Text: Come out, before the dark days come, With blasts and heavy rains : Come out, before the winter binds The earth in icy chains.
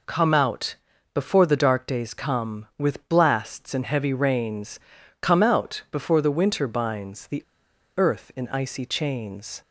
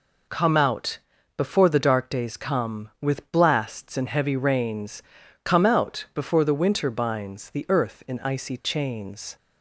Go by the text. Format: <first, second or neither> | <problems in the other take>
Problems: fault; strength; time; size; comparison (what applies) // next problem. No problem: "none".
second | pauses between "The" and "earth"; noticeable; at 7.4 s; 0.57 s long